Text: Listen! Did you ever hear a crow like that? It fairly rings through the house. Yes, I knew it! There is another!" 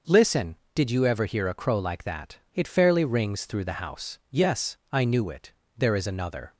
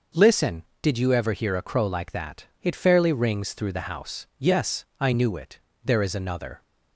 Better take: neither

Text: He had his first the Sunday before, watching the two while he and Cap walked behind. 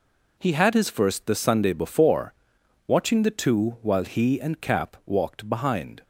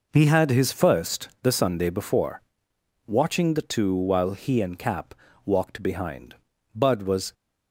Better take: first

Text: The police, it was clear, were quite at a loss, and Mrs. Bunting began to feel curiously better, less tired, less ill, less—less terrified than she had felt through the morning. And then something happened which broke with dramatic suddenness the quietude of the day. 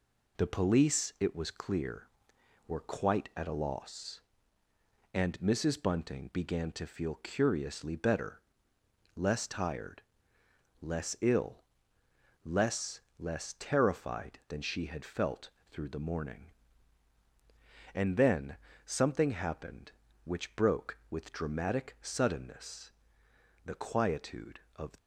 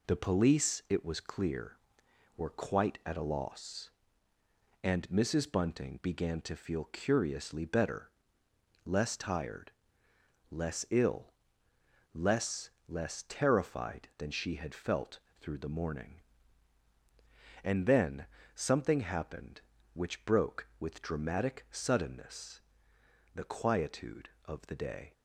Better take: second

